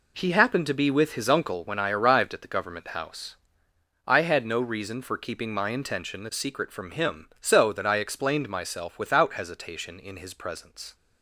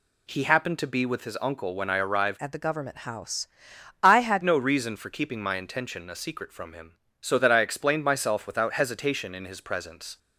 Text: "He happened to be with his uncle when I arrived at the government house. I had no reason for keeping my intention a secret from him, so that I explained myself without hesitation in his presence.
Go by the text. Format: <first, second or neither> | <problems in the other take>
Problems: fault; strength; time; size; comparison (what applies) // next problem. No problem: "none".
first | changes voice from "at" to "had"; from 2.4 to 4.4 s; 2.0 s long